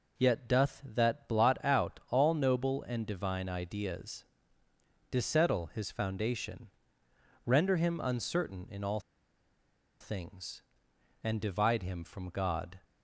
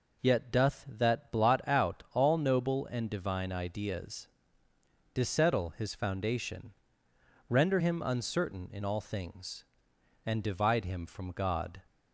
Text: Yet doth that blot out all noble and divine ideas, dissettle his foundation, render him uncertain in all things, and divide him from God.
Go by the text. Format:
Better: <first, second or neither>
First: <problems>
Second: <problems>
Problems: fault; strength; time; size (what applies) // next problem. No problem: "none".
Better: second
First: pauses between "all" and "things"; at 8.9 s; 1.0 s long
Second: none